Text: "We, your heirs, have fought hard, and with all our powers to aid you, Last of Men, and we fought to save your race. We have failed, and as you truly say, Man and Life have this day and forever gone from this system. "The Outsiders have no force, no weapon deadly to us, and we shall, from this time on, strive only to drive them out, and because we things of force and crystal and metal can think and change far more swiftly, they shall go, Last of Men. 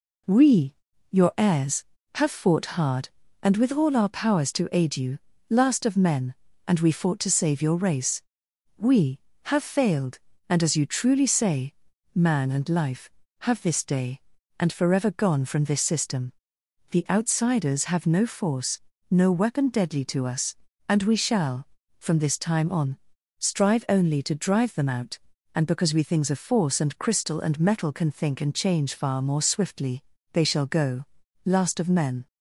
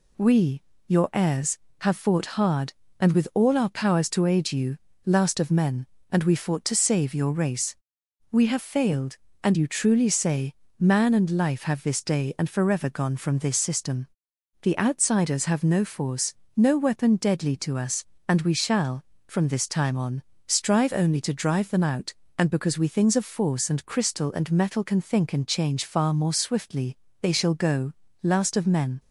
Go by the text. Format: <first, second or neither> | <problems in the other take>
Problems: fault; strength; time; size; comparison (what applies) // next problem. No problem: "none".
first | skips "as"; at 9.5 s